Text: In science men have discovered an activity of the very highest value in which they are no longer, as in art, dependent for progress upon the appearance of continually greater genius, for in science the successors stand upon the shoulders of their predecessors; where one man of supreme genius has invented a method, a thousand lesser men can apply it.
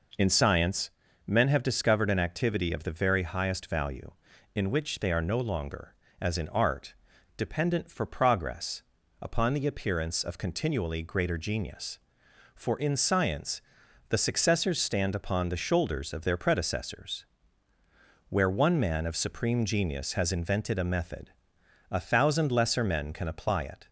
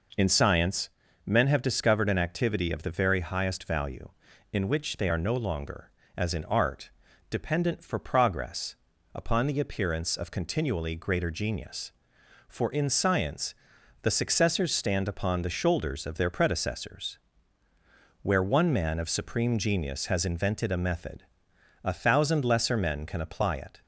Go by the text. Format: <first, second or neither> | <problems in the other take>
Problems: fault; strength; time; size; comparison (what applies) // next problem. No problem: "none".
neither | pauses between "science" and "men"; slight; the same in both // pauses between "progress" and "upon"; the same in both // pauses between "science" and "the"; noticeable; the same in both